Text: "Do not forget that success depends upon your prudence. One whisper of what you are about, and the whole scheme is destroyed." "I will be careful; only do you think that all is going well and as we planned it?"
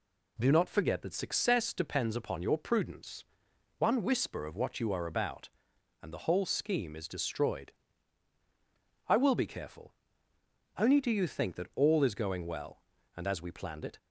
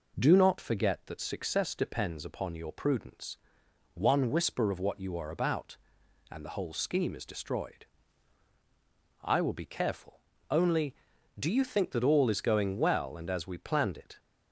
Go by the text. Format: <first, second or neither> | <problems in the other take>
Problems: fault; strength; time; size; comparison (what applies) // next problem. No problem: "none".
neither | none